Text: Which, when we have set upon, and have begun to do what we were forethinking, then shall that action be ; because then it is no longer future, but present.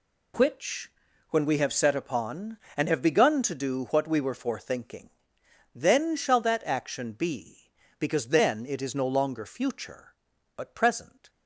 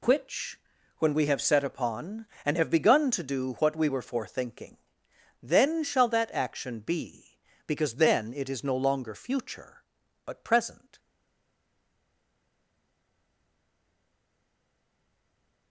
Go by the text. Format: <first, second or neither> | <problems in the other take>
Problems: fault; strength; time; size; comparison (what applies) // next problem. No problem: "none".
first | stays silent after the last word; strong; from 10.9 s on; 4.7 s long